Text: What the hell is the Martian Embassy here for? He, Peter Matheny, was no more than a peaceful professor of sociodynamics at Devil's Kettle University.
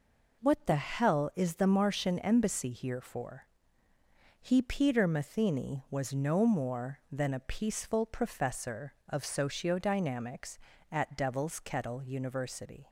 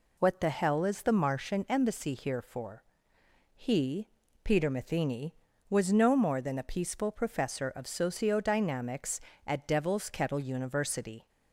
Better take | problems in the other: neither | none

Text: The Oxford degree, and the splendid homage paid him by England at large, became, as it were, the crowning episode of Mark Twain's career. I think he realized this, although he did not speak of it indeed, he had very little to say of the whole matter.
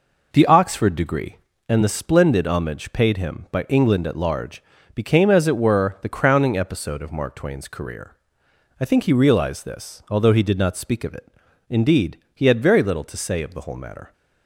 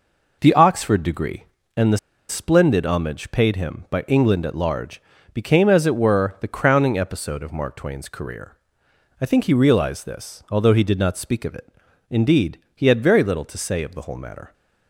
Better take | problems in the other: first | pauses between "the" and "splendid"; slight; at 1.9 s; 0.32 s long // pauses between "it" and "indeed"; at 11.6 s; 0.40 s long; also in the first

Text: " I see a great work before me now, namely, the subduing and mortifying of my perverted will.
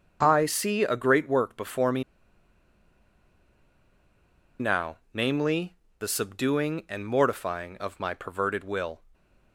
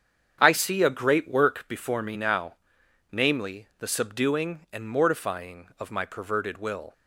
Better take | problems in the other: second | starts louder than the rest; until 1.2 s; 6.5 dB; strong in the second // pauses between "me" and "now"; strong; at 2.0 s; 2.5 s long

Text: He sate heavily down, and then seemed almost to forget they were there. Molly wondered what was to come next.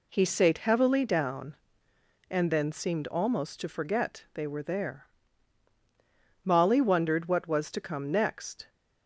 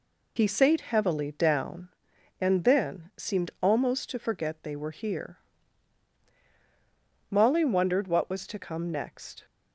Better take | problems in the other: first | says "here" for "there"; at 4.9 s

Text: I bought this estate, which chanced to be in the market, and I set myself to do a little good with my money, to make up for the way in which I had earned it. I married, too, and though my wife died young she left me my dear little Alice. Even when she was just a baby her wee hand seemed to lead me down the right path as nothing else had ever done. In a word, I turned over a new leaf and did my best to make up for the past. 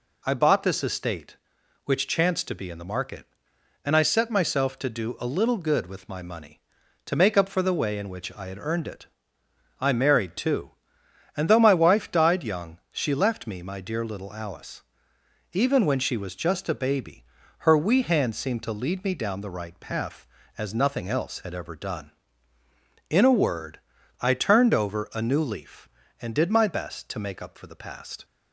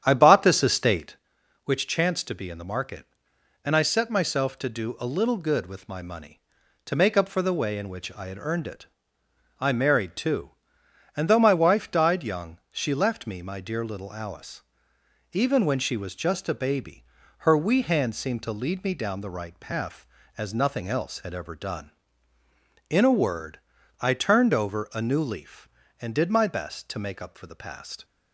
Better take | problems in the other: first | starts louder than the rest; strong; until 1.2 s; 9.5 dB // pauses between "baby" and "her"; slight; at 17.0 s; 0.36 s long; slight in the first

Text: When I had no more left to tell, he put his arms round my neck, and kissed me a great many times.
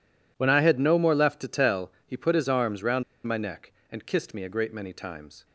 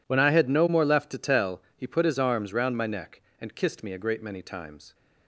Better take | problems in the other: second | pauses between "round" and "my"; slight; at 3.0 s; 0.23 s long

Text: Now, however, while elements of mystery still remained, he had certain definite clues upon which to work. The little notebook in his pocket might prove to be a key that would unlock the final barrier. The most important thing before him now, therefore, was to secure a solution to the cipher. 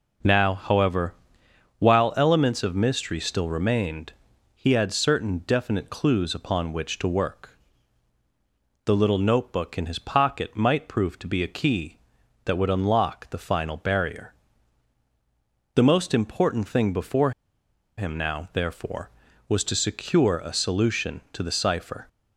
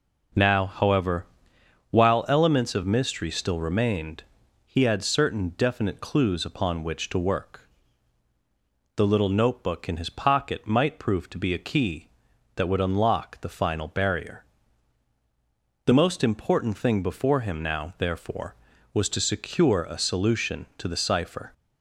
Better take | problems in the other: second | pauses between "before" and "him"; noticeable; at 17.3 s; 0.66 s long

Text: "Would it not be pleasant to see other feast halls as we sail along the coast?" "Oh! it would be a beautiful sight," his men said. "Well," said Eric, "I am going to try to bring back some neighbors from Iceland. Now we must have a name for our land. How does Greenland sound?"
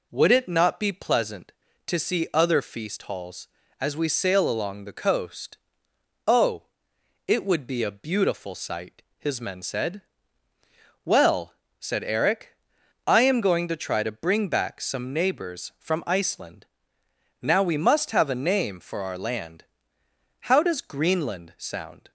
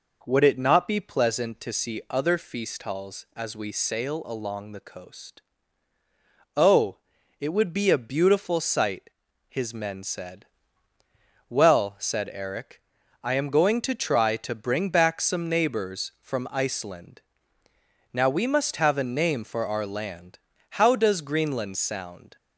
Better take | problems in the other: neither | none

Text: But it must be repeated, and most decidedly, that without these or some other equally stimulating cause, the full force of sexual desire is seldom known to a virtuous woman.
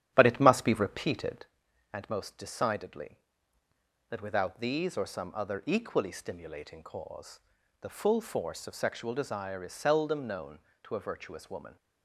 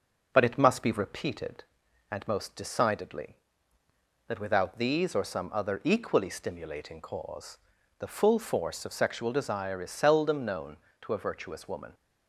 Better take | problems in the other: second | starts louder than the rest; strong; until 1.5 s; 10.5 dB

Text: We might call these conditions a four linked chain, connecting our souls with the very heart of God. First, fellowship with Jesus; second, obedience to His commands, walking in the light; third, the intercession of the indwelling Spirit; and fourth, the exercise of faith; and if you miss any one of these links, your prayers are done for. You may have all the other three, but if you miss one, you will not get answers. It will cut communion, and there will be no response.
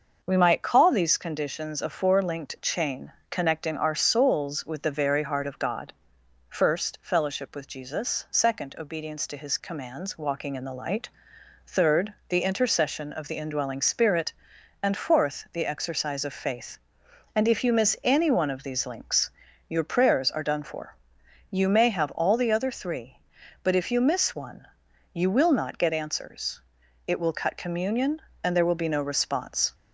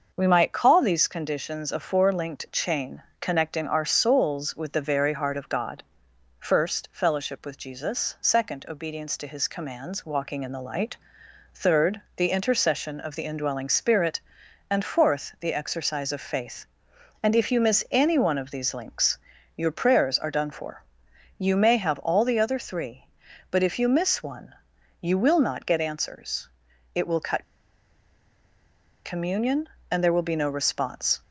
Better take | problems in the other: first | starts louder than the rest; noticeable; until 1.1 s; 6 dB; noticeable in the first // pauses between "cut" and "communion"; strong; at 27.4 s; 1.6 s long

